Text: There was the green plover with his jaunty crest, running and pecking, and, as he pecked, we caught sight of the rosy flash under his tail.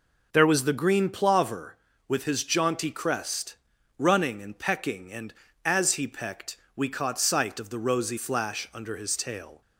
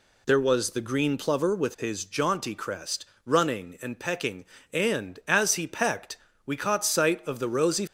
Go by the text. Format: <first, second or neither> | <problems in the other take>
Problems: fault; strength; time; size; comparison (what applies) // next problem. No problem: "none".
first | stops before "flash under his tail"; at 7.8 s